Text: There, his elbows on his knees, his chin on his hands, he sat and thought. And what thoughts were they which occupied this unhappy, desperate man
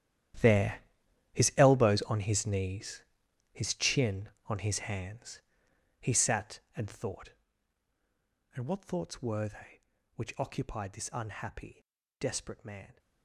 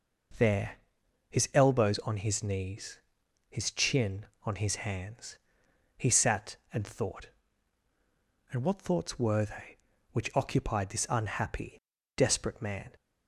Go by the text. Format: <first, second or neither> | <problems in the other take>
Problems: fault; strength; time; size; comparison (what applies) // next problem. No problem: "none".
second | gets quieter; strong; throughout; 16.5 dB